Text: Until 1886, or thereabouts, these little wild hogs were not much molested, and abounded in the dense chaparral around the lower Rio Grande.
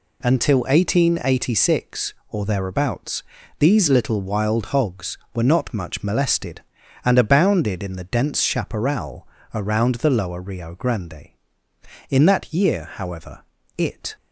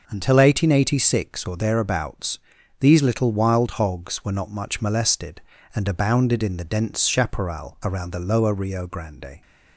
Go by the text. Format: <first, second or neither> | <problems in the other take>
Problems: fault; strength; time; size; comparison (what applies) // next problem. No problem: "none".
second | pauses between "chaparral" and "around"; slight; at 9.2 s; 0.26 s long // goes on to say "In that year however it"; strong; from 12.0 s on; 2.0 s long